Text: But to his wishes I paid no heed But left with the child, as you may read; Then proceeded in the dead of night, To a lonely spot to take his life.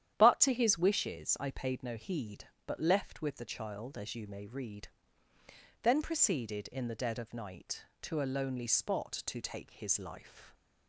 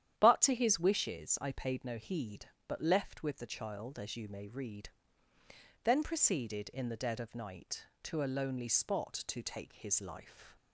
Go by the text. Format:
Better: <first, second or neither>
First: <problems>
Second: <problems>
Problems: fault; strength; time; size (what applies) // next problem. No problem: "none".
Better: neither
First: starts louder than the rest; strong; until 1.1 s; 10.5 dB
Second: starts louder than the rest; strong; until 1.2 s; 10 dB